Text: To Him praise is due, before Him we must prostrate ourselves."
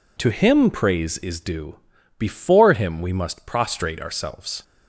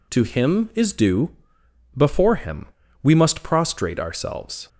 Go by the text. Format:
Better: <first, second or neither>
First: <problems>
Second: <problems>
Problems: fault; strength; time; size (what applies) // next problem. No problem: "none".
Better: first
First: none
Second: skips "praise"; at 0.7 s // pauses between "Him" and "we"; slight; at 2.6 s; 0.36 s long